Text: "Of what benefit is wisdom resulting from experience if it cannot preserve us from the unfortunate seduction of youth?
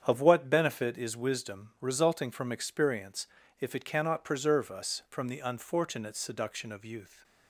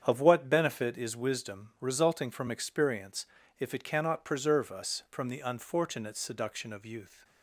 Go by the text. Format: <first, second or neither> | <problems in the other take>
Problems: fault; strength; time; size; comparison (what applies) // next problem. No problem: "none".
neither | starts louder than the rest; strong; the same in both // pauses between "experience" and "if"; slight; the same in both